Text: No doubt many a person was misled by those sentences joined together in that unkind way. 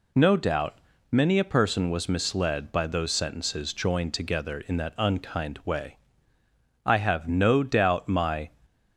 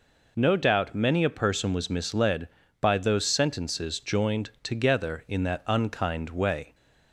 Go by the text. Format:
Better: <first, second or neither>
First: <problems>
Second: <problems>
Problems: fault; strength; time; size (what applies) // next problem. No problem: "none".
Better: second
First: pauses between "doubt" and "many"; slight; at 0.7 s; 0.32 s long // goes on to say "I have no doubt my"; from 6.8 s on; 1.6 s long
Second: none